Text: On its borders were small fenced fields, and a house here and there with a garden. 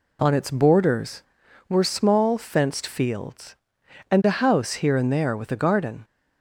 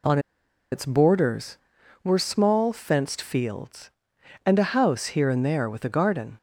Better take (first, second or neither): first